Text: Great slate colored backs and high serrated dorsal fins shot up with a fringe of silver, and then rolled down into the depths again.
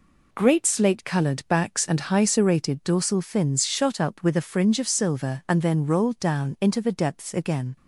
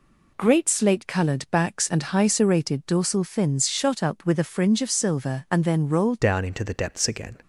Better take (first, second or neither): first